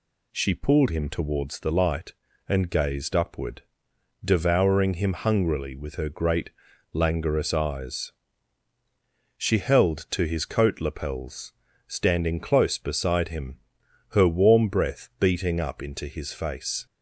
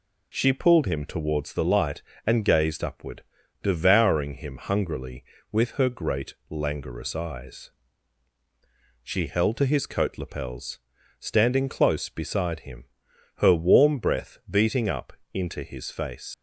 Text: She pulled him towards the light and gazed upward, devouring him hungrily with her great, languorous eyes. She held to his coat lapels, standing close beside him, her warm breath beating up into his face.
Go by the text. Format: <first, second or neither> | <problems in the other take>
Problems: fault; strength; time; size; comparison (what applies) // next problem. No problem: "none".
first | pauses between "up" and "into"; slight; at 15.1 s; 0.22 s long // leaves "face" unfinished; at 16.3 s; 85 ms